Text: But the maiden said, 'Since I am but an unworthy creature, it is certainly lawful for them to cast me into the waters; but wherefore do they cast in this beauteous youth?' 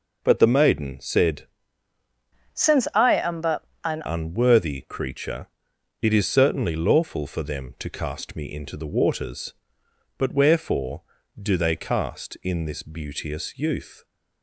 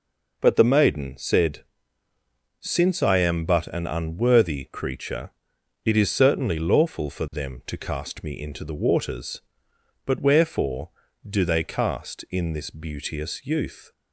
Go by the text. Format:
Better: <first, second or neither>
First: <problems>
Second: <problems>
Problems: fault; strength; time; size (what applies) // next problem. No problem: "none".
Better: second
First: changes voice from "Since" to "an"; from 2.5 to 4.0 s; 1.5 s long // pauses between "but" and "an"; slight; at 3.6 s; 0.22 s long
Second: none